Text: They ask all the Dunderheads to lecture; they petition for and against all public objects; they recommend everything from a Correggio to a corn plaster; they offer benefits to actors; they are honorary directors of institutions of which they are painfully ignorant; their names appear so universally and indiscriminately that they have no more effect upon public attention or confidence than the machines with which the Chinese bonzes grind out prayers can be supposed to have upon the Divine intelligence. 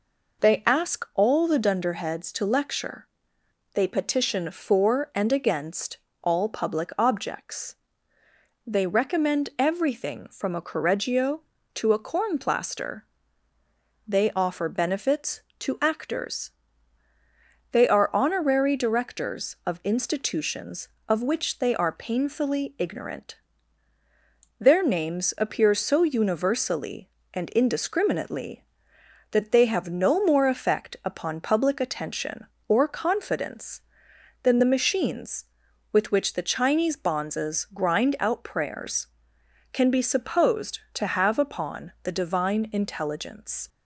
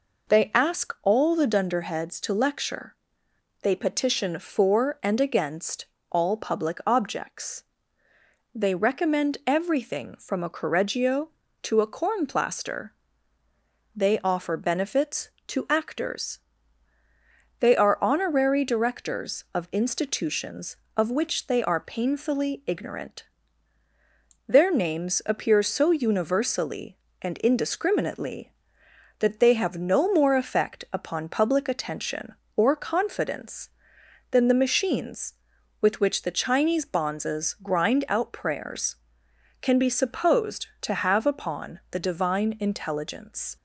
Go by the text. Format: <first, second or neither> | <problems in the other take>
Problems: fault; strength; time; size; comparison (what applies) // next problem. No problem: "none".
neither | pauses between "against" and "all"; slight; the same in both